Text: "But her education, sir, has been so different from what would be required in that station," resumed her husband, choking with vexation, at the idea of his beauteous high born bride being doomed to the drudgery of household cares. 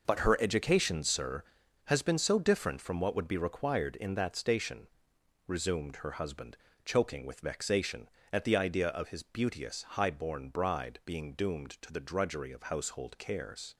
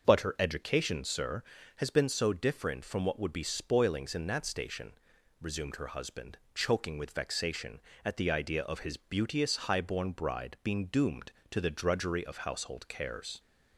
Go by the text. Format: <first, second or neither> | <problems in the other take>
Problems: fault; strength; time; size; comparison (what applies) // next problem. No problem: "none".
first | starts louder than the rest; until 1.0 s; 6 dB // says "spoilings" for "required"; at 3.4 s